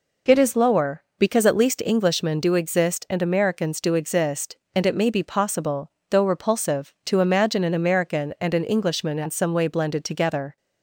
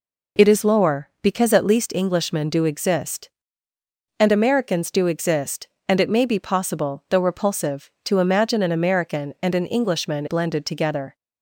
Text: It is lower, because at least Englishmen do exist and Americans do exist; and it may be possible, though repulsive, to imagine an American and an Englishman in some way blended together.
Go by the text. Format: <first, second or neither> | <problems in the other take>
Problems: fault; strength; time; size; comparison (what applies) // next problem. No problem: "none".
first | skips "in some way"; at 10.2 s